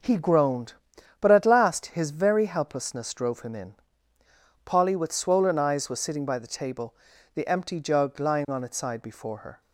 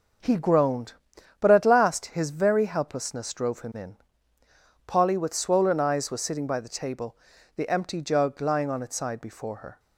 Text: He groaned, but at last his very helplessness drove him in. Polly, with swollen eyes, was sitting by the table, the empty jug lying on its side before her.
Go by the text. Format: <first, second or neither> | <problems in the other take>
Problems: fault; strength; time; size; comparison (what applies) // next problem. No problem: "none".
neither | none